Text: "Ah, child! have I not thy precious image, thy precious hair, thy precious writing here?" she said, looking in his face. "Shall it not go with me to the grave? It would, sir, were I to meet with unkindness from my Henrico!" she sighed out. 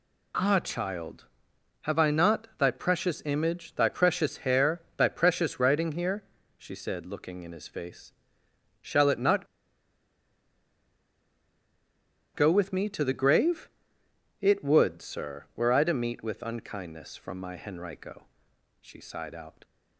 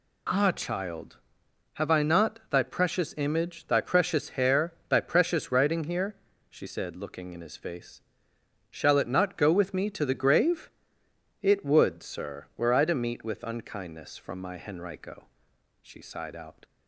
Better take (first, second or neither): second